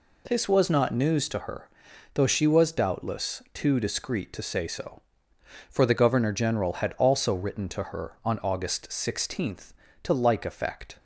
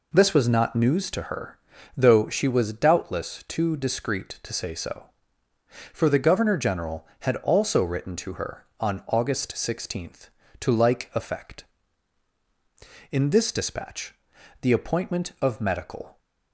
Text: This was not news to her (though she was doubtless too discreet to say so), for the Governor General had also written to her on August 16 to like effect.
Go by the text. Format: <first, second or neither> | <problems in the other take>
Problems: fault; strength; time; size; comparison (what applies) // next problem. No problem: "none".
first | goes on to say "In this dispatch the appointment of medical"; strong; from 13.1 s on; 3.0 s long